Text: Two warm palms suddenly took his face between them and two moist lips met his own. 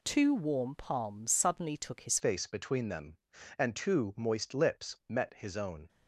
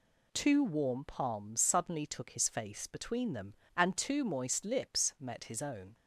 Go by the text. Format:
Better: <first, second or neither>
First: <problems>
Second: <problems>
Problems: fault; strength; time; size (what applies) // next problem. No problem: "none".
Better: second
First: changes voice at "face"; from 2.1 s on; 3.7 s long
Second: none